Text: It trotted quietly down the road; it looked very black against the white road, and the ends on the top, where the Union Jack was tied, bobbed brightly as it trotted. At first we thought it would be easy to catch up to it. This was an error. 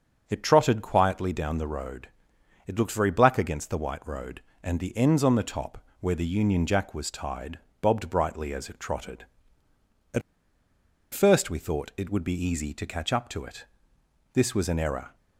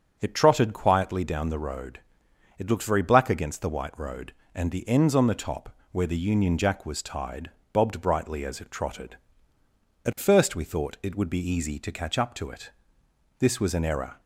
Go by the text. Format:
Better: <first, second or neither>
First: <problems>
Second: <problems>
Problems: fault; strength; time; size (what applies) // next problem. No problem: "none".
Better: second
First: starts louder than the rest; strong; until 1.2 s; 7.5 dB // pauses between "At" and "first"; noticeable; at 10.2 s; 0.92 s long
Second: starts louder than the rest; strong; until 1.2 s; 7.5 dB